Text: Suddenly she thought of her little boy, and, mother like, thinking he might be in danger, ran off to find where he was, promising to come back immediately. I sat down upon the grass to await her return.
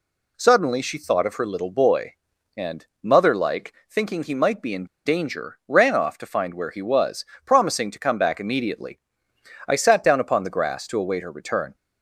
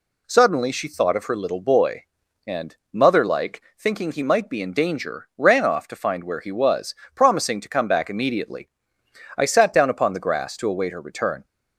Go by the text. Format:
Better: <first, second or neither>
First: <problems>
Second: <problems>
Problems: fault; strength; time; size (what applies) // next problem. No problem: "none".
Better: second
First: pauses between "in" and "danger"; slight; at 4.8 s; 0.21 s long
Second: none